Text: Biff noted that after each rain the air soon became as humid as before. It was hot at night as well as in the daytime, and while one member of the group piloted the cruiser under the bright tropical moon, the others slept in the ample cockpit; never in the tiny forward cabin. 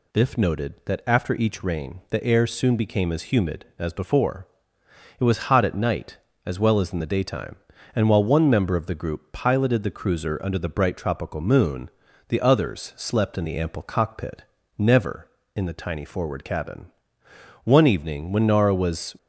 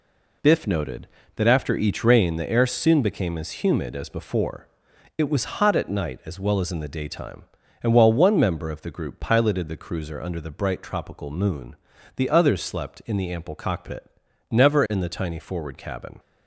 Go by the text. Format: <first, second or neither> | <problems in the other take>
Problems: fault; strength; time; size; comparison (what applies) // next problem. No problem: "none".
second | goes on to say "One evening when Nara was"; from 17.6 s on; 1.5 s long